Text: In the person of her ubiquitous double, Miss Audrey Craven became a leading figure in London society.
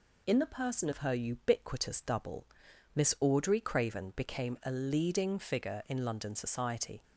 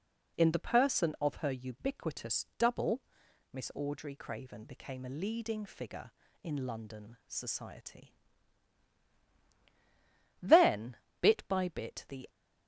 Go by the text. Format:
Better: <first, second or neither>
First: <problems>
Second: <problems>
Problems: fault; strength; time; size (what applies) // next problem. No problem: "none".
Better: first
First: none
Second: goes on to say "Then bit by bit the"; strong; from 10.4 s on; 1.8 s long